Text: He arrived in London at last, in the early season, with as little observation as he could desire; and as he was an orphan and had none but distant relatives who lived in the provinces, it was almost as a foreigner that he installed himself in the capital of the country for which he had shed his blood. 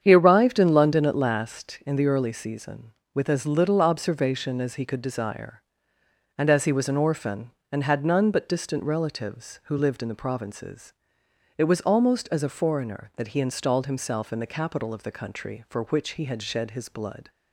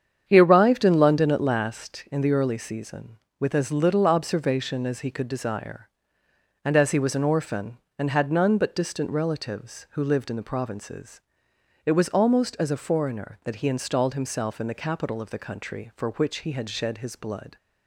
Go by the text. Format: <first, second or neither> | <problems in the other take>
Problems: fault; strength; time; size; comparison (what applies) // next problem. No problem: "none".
neither | starts louder than the rest; strong; the same in both